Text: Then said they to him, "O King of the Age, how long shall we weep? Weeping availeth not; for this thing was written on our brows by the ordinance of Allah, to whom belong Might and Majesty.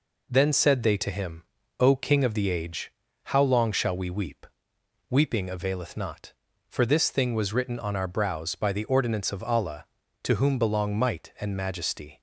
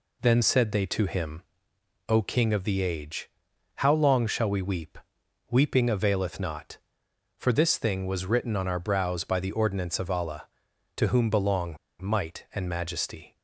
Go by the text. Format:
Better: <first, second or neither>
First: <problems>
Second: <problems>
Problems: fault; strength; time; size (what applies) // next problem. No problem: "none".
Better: first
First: none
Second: pauses between "belong" and "Might"; slight; at 11.7 s; 0.24 s long